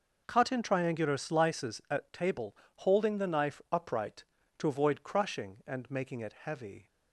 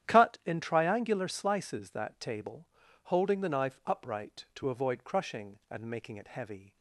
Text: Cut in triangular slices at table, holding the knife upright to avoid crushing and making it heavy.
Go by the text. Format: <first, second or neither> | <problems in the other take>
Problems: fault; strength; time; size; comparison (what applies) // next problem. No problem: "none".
first | starts louder than the rest; strong; until 1.1 s; 10.5 dB // says "that" for "at"; at 1.8 s